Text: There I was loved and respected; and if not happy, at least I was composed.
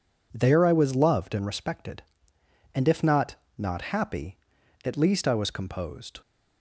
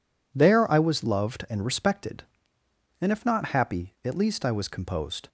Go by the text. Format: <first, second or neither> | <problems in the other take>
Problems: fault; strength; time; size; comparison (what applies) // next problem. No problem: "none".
second | says "not" twice; at 3.5 s